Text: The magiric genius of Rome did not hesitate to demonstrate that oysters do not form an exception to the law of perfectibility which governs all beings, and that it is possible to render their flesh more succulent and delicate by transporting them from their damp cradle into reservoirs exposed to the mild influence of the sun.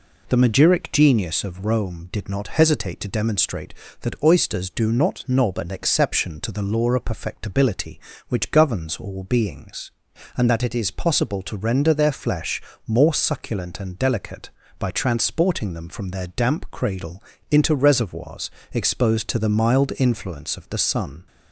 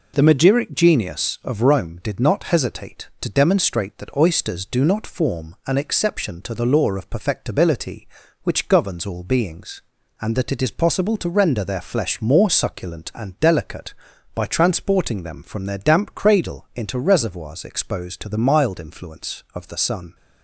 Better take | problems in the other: second | says "knob" for "form"; at 5.2 s // pauses between "flesh" and "more"; slight; at 12.6 s; 0.28 s long // pauses between "cradle" and "into"; slight; at 17.2 s; 0.30 s long // pauses between "reservoirs" and "exposed"; slight; at 18.5 s; 0.22 s long

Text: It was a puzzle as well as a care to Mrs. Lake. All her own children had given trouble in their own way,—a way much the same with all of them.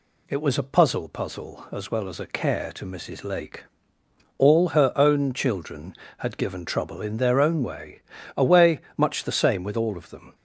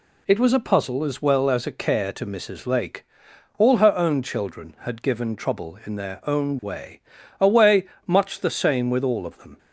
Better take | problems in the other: second | says "puzzle" twice; at 1.0 s // pauses between "way" and "much"; slight; at 8.7 s; 0.18 s long; slight in the second

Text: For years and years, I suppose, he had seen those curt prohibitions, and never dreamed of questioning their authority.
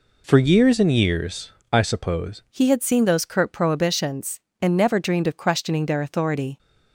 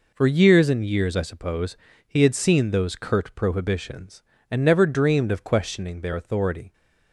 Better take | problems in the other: second | changes voice at "he"; from 2.5 s on; 4.0 s long

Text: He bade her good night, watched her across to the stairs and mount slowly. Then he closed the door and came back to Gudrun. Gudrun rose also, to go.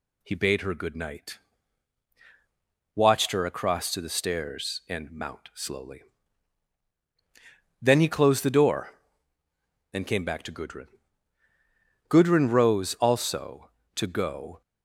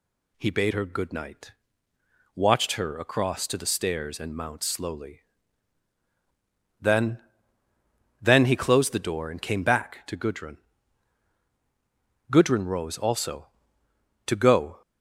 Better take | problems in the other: first | says "Then" twice; at 8.2 s

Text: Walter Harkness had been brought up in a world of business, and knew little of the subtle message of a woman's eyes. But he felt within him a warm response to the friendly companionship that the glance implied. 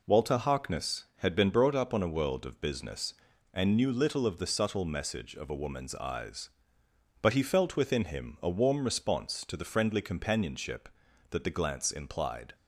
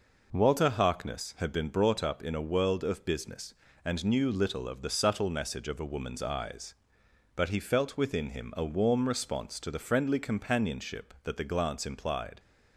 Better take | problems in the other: second | says "on" for "in"; at 1.9 s

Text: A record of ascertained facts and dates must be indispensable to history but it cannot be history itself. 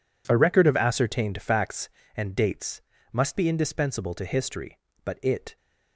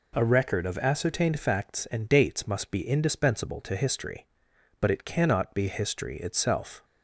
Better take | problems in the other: second | pauses between "dates" and "must"; slight; at 2.8 s; 0.30 s long // stops before "cannot be history itself"; at 5.5 s

